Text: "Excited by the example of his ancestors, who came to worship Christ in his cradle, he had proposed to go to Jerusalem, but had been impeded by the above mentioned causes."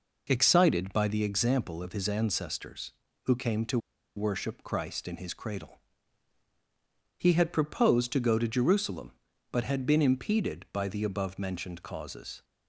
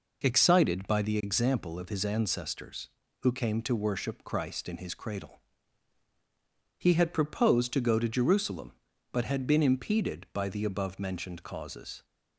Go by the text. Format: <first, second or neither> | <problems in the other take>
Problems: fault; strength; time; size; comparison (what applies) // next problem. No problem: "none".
second | pauses between "to" and "worship"; at 3.7 s; 0.38 s long